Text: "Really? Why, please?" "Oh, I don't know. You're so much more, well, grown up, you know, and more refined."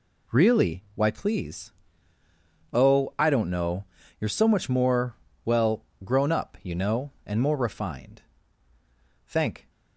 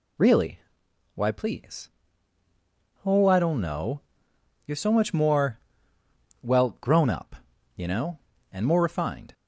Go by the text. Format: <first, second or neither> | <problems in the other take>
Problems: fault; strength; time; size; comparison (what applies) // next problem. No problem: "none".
second | goes on to say "Thank"; slight; from 9.2 s on; 0.44 s long